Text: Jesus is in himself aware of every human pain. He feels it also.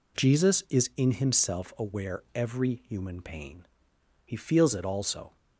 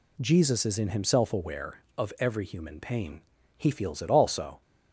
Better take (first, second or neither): second